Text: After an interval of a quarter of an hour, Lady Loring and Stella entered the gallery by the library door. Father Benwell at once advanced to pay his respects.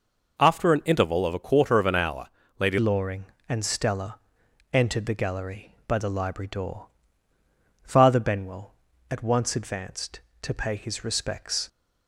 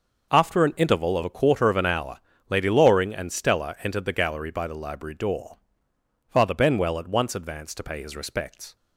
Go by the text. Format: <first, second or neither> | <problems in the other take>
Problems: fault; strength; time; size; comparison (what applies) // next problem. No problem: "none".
second | changes voice at "Loring"; from 2.7 s on; 8.9 s long // pauses between "Stella" and "entered"; noticeable; at 4.1 s; 0.54 s long